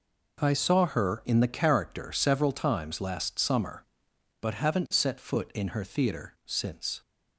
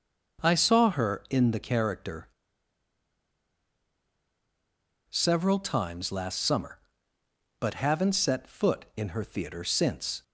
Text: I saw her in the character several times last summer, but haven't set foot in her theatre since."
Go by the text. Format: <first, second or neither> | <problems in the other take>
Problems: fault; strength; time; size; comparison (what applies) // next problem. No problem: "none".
first | pauses between "character" and "several"; strong; at 2.2 s; 2.8 s long